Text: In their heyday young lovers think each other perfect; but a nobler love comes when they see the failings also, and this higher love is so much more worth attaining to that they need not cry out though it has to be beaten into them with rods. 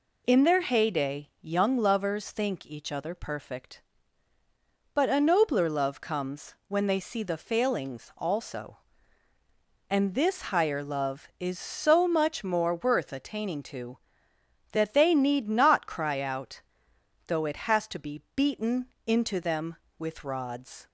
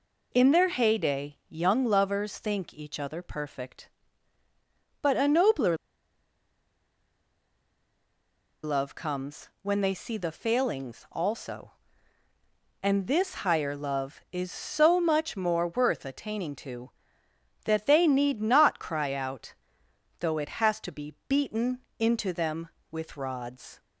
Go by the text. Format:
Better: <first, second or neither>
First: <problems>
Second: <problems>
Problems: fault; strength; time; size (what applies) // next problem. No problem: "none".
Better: first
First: pauses between "out" and "though"; noticeable; at 16.5 s; 0.68 s long // pauses between "beaten" and "into"; slight; at 18.8 s; 0.18 s long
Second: pauses between "nobler" and "love"; strong; at 5.7 s; 2.8 s long // pauses between "out" and "though"; noticeable; at 19.5 s; 0.68 s long // pauses between "beaten" and "into"; slight; at 21.8 s; 0.18 s long